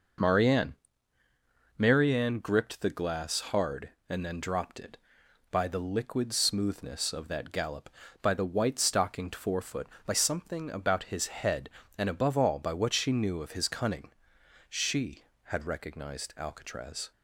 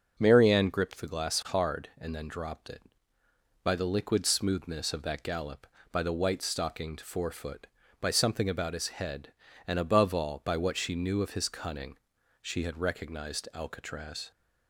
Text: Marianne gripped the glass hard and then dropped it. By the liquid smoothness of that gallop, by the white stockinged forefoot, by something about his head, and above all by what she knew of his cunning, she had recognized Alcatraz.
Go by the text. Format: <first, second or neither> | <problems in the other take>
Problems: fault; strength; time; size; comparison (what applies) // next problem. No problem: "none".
second | says "Marianne" twice; at 1.7 s